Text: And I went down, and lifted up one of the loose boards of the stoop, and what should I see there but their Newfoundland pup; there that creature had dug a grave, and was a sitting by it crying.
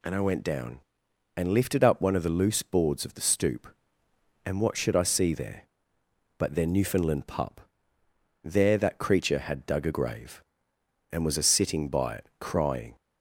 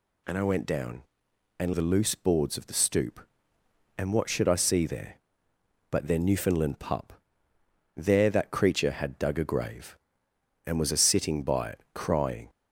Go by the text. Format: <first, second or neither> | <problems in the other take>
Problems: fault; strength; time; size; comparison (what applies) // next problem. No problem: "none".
first | skips "lifted up one of"; at 1.7 s